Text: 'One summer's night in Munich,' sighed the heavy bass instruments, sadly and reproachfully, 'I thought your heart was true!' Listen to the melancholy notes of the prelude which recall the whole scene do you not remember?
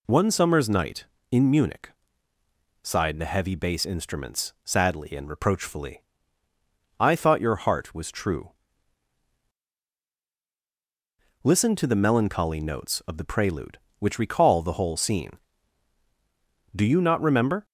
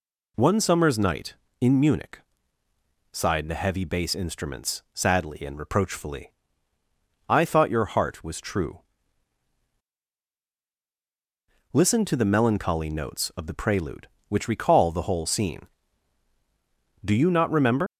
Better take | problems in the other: first | leaves "remember" unfinished; at 17.8 s; 80 ms

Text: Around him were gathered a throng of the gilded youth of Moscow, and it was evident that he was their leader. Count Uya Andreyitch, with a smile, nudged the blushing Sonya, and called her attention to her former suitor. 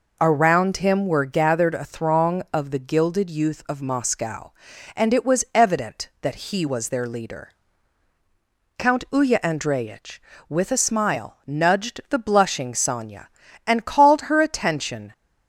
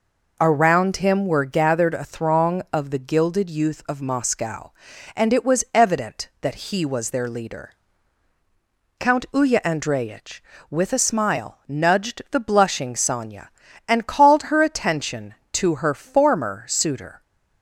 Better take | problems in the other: second | stops before "to her former suitor"; at 15.1 s

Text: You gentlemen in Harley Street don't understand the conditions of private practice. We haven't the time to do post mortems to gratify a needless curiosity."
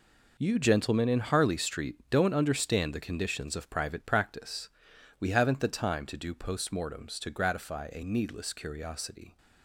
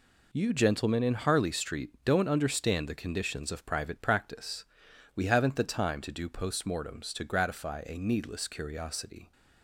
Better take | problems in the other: second | gets quieter; strong; throughout; 12.5 dB // pauses between "Street" and "don't"; slight; at 1.9 s; 0.16 s long; slight in the second

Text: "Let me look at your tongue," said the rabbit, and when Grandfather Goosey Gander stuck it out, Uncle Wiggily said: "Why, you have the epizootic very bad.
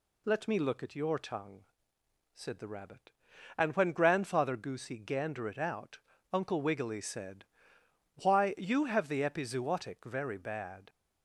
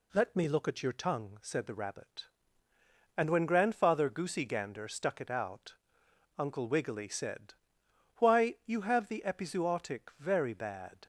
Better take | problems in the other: second | skips "stuck"; at 5.4 s

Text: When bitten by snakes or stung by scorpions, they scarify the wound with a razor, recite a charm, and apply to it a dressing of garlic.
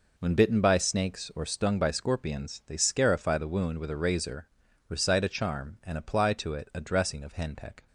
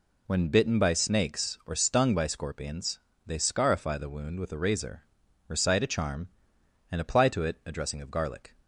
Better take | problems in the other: second | says "henpeck" for "garlic"; at 7.3 s

